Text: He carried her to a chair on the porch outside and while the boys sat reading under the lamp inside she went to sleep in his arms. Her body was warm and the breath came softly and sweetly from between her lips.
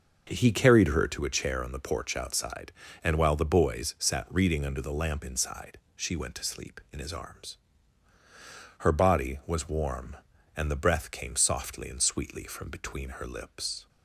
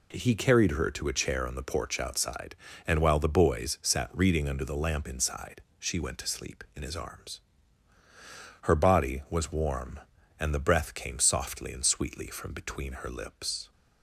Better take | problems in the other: second | starts louder than the rest; noticeable; until 1.2 s; 6 dB // pauses between "inside" and "she"; slight; at 5.7 s; 0.18 s long; slight in the second

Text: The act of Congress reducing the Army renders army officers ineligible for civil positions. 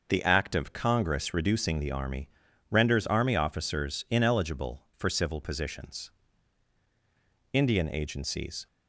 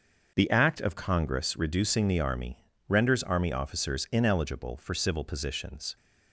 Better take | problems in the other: second | starts louder than the rest; noticeable; until 1.0 s; 6 dB; also in the second // pauses between "Army" and "renders"; at 2.2 s; 0.42 s long; slight in the second // goes on to say "Indian agencies"; noticeable; from 7.5 s on; 1.1 s long

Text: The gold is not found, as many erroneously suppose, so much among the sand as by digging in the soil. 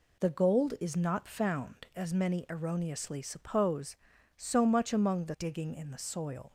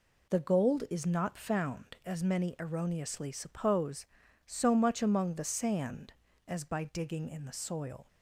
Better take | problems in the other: second | skips "sand as by"; at 5.3 s

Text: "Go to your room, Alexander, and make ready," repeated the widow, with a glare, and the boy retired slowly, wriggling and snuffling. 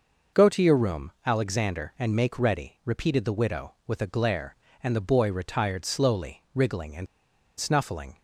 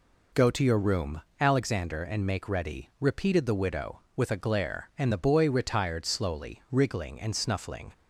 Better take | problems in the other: second | pauses between "and" and "snuffling"; noticeable; at 7.0 s; 0.51 s long

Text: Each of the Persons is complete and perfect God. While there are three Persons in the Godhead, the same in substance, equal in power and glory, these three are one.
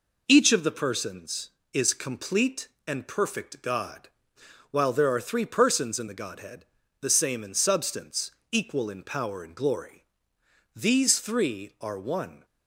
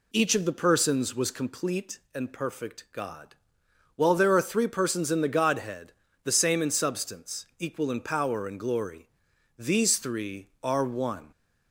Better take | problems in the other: first | says "was" for "is"; at 1.1 s

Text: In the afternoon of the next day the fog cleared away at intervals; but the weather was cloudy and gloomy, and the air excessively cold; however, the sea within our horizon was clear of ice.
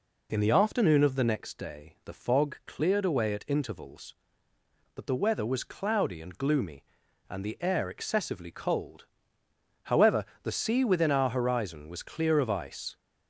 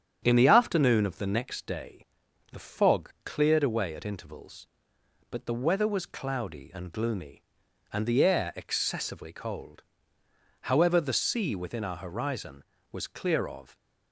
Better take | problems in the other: first | starts louder than the rest; strong; until 1.2 s; 8.5 dB // pauses between "day" and "the"; noticeable; at 2.0 s; 0.48 s long // stops before "ice"; at 13.7 s

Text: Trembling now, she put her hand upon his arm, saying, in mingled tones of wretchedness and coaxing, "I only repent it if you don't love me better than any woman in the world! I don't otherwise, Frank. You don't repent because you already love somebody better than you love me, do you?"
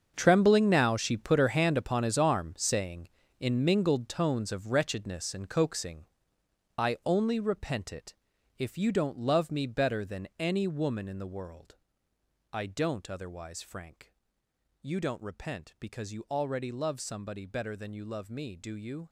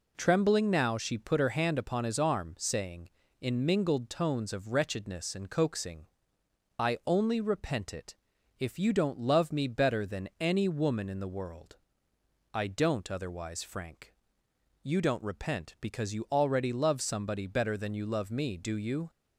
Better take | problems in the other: second | gets quieter; strong; throughout; 14 dB // pauses between "it" and "if"; at 8.1 s; 0.42 s long; also in the second

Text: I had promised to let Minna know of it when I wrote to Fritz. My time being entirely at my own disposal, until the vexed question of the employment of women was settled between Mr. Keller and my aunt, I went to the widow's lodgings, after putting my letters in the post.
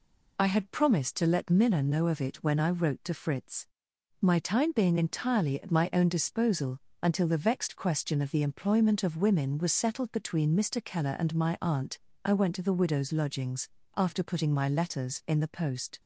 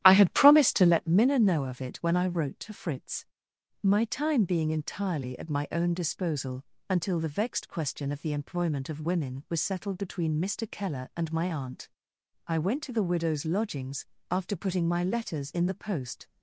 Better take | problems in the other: first | starts louder than the rest; strong; until 1.1 s; 12.5 dB

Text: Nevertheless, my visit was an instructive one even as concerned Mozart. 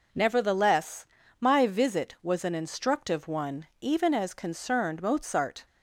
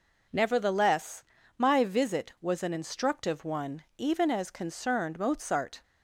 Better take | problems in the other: neither | none

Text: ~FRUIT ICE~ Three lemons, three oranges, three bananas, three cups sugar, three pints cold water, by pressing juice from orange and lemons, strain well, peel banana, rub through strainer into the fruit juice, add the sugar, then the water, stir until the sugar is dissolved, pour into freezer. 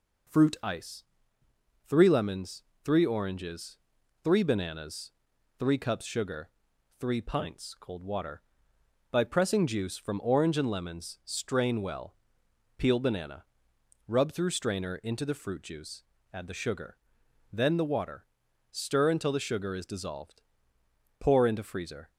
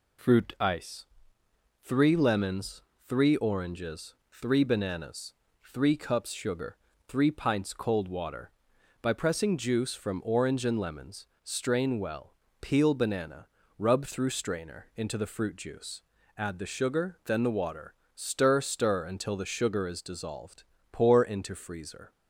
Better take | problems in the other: first | says "stir" twice; at 18.5 s

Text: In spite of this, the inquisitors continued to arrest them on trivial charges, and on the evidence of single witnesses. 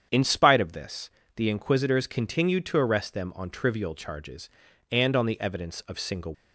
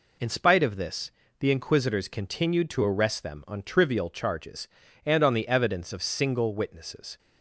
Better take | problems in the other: second | starts louder than the rest; strong; until 1.3 s; 8.5 dB // stops before "witnesses"; at 6.3 s

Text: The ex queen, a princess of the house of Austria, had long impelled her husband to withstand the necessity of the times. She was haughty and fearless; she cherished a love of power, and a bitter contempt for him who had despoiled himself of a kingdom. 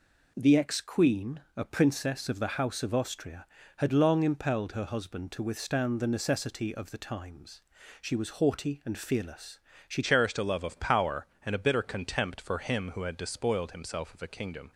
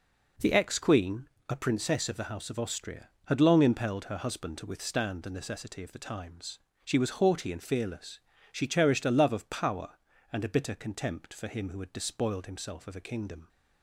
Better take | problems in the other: second | changes voice at "cherished"; from 10.0 s on; 4.7 s long

